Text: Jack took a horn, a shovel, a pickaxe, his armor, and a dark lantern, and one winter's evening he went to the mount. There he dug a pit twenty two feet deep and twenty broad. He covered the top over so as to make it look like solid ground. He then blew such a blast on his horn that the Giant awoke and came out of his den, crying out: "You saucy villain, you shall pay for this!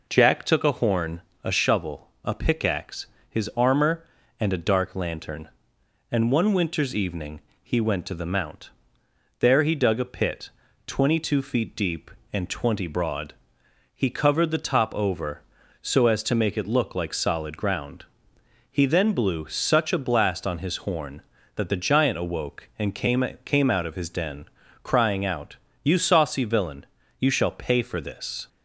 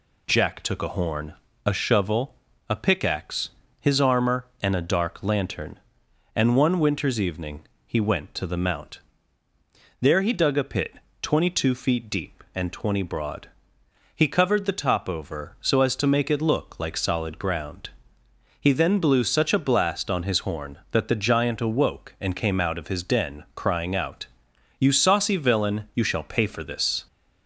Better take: second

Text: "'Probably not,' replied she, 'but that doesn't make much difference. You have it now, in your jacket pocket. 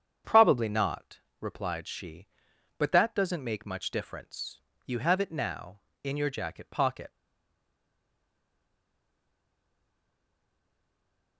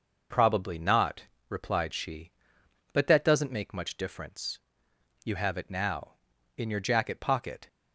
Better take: second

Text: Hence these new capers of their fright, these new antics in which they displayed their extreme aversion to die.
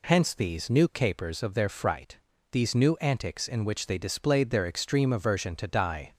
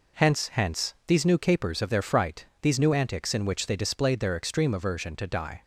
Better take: first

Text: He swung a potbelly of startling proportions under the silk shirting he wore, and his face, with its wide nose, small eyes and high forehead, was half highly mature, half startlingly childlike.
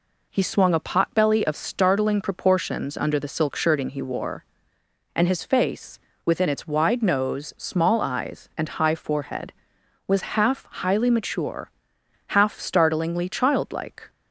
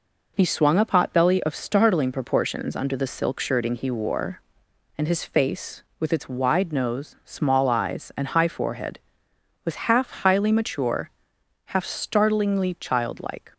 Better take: second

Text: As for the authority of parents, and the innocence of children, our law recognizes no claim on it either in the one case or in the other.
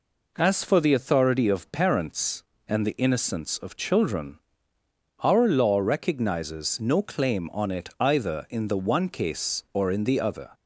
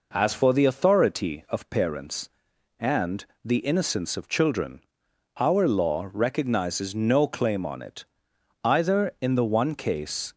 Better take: first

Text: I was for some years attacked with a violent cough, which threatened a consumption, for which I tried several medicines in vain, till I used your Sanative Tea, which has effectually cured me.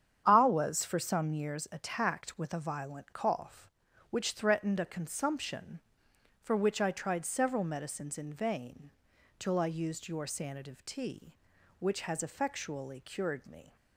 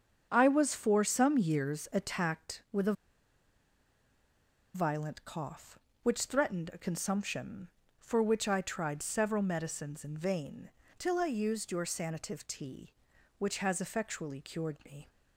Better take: first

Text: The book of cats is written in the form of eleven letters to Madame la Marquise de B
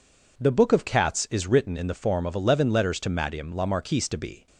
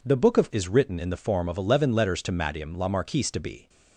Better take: first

